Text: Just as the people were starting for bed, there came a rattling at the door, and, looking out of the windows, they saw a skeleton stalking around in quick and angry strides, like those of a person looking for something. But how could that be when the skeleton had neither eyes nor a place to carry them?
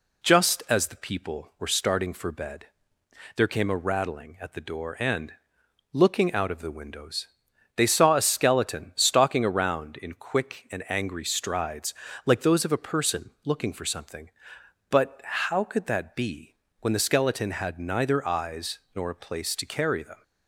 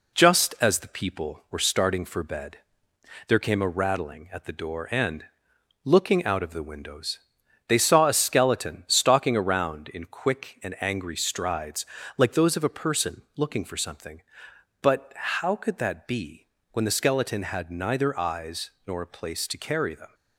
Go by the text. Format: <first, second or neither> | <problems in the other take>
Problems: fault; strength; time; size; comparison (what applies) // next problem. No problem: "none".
first | gets quieter; throughout; 3.5 dB // pauses between "be" and "when"; slight; at 16.4 s; 0.26 s long; slight in the first // pauses between "eyes" and "nor"; slight; at 18.7 s; 0.16 s long; slight in the first